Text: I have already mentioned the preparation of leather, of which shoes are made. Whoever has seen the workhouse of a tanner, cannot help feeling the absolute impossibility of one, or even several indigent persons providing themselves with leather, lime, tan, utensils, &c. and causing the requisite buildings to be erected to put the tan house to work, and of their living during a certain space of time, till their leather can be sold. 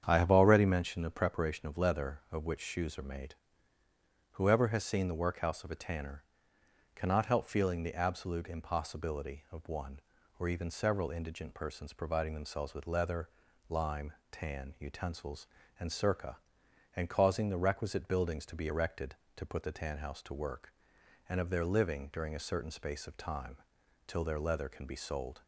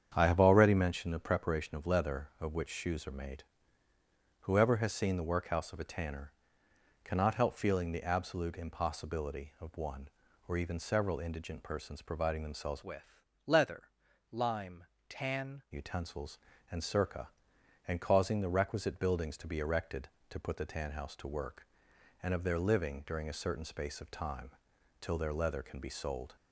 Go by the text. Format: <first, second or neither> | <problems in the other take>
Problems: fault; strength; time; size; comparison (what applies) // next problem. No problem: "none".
first | starts louder than the rest; strong; until 1.1 s; 8 dB; strong in the first // changes voice from "with" to "tan"; from 12.8 to 15.6 s; 2.8 s long // pauses between "with" and "leather"; slight; at 13.1 s; 0.26 s long